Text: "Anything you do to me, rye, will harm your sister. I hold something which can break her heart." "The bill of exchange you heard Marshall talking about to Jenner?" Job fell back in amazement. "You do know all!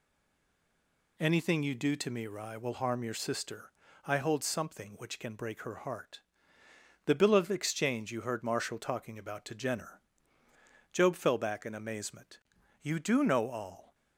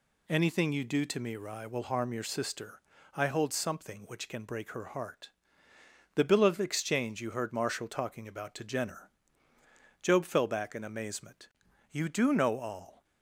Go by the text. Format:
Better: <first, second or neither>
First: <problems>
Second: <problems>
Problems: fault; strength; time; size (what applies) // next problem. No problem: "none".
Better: second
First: stays silent before the first word; noticeable; until 1.1 s; 1.1 s long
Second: none